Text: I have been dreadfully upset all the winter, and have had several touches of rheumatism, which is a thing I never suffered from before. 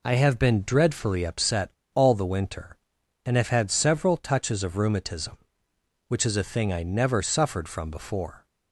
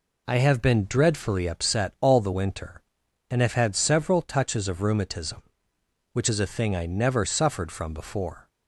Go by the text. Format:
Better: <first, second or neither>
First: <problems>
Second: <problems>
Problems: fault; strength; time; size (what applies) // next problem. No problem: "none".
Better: second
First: pauses between "upset" and "all"; slight; at 1.7 s; 0.22 s long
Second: none